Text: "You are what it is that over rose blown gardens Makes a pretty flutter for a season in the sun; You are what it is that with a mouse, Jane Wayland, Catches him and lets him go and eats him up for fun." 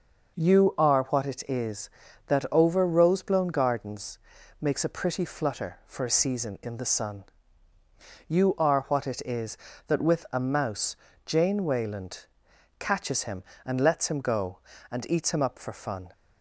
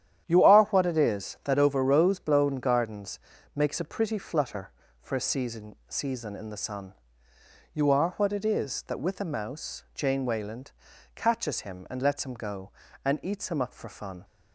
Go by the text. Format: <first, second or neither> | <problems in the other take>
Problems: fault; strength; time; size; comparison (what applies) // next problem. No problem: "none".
first | starts louder than the rest; strong; until 1.2 s; 10.5 dB // pauses between "gardens" and "Makes"; slight; at 3.1 s; 0.36 s long; also in the first // says "season" twice; at 5.8 s